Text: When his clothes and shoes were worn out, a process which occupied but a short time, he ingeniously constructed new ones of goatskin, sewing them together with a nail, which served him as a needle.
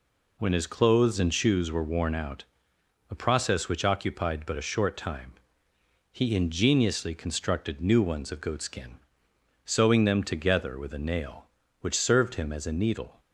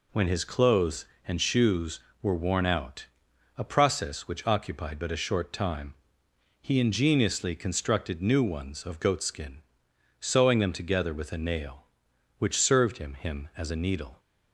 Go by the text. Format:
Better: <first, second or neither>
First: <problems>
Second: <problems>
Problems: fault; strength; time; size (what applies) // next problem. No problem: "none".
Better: first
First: none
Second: says "him" twice; at 13.1 s